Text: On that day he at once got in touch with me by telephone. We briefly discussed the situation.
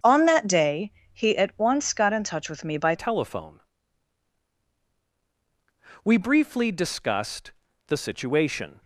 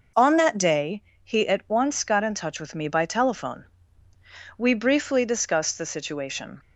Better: second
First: starts louder than the rest; strong; until 1.2 s; 7 dB // pauses between "day" and "he"; slight; at 0.9 s; 0.20 s long // changes voice at "telephone"; from 2.9 s on; 5.9 s long // pauses between "discussed" and "the"; at 7.5 s; 0.38 s long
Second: pauses between "day" and "he"; slight; at 1.0 s; 0.20 s long

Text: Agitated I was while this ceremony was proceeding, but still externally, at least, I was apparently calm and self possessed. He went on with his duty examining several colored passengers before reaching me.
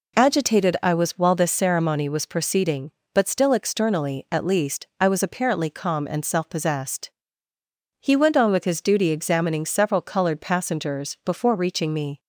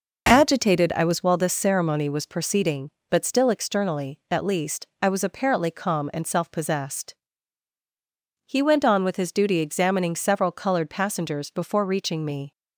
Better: neither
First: none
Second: none

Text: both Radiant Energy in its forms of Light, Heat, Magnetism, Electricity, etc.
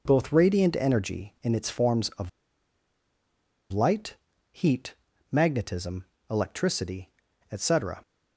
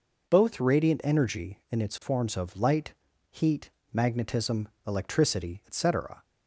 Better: second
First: pauses between "of" and "Light"; strong; at 2.2 s; 1.4 s long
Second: none

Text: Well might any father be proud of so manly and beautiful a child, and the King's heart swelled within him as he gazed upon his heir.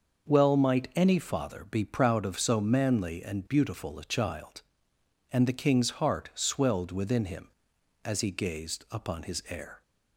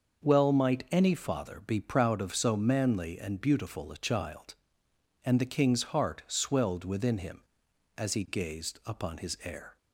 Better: neither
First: starts louder than the rest; until 1.3 s; 6 dB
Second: starts louder than the rest; until 1.2 s; 6 dB

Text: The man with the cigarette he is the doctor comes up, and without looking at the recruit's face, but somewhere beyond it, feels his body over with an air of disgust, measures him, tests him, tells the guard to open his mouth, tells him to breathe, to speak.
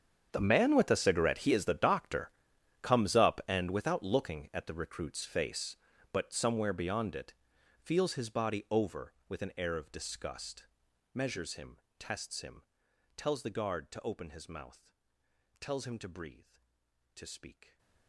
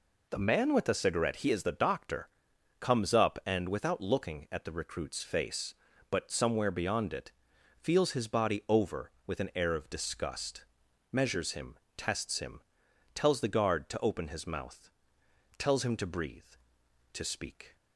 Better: second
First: gets quieter; strong; throughout; 19 dB // pauses between "doctor" and "comes"; noticeable; at 2.2 s; 0.52 s long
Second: pauses between "doctor" and "comes"; noticeable; at 2.2 s; 0.52 s long

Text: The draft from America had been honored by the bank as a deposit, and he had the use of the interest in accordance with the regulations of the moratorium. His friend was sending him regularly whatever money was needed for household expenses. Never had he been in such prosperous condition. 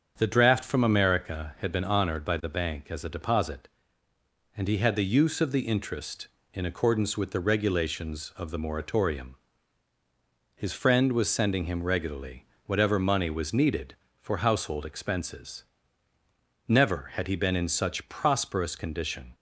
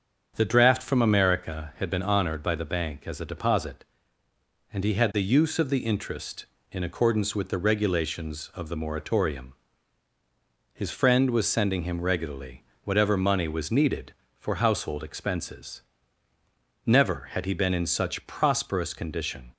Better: neither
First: starts louder than the rest; strong; until 1.1 s; 7 dB // pauses between "regularly" and "whatever"; slight; at 12.4 s; 0.20 s long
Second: starts louder than the rest; strong; until 1.3 s; 7 dB // pauses between "regularly" and "whatever"; slight; at 12.6 s; 0.20 s long

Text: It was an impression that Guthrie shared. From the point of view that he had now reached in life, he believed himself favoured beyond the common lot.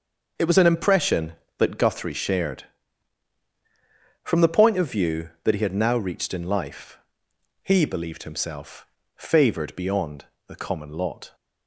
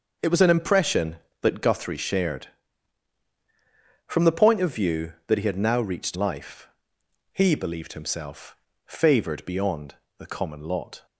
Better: first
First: starts louder than the rest; until 1.6 s; 6 dB // pauses between "himself" and "favoured"; slight; at 8.8 s; 0.30 s long // pauses between "beyond" and "the"; slight; at 10.2 s; 0.21 s long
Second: starts louder than the rest; until 1.4 s; 6 dB // skips "in"; at 6.1 s // pauses between "himself" and "favoured"; slight; at 8.5 s; 0.30 s long // pauses between "beyond" and "the"; slight; at 9.9 s; 0.22 s long

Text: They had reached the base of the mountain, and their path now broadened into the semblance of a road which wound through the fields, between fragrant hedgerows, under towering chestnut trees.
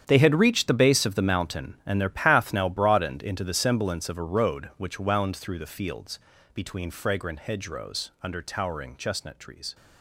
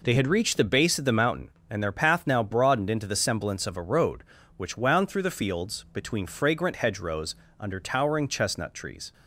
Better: second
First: gets quieter; strong; throughout; 13.5 dB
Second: none

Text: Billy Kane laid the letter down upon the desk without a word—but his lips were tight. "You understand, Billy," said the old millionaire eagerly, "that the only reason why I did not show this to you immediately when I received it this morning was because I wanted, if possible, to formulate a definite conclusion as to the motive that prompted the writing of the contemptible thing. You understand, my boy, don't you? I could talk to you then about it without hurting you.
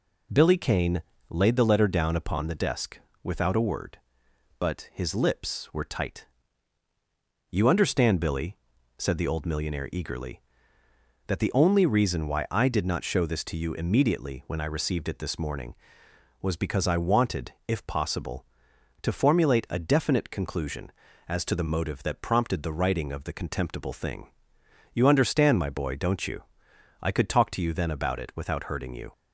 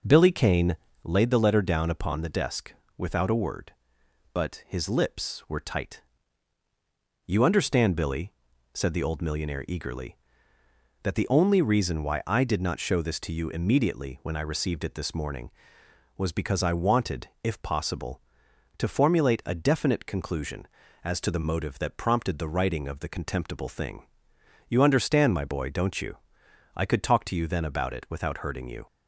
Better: first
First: pauses between "Kane" and "laid"; slight; at 1.0 s; 0.26 s long // pauses between "desk" and "without"; slight; at 2.9 s; 0.24 s long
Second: starts louder than the rest; noticeable; until 1.0 s; 5 dB // pauses between "Kane" and "laid"; slight; at 0.7 s; 0.26 s long // pauses between "desk" and "without"; slight; at 2.7 s; 0.24 s long

